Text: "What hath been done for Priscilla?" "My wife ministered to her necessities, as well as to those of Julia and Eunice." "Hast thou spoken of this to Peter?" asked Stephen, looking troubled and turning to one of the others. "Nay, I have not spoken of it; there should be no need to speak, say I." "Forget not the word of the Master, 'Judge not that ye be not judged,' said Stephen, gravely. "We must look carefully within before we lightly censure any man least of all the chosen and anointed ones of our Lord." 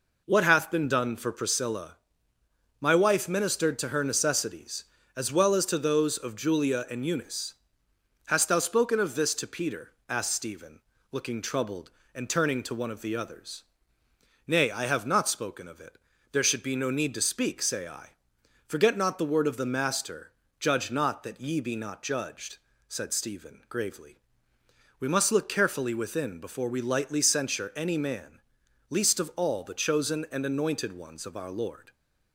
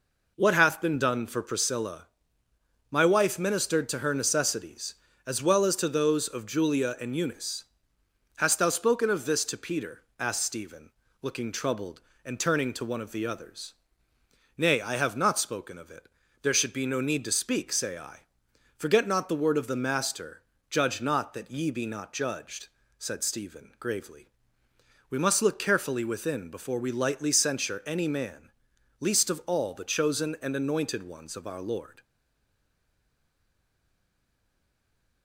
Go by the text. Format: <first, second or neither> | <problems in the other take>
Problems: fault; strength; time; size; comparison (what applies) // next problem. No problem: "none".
first | pauses between "man" and "least"; noticeable; at 28.4 s; 0.50 s long; noticeable in the first // stays silent after the last word; strong; from 32.0 s on; 3.2 s long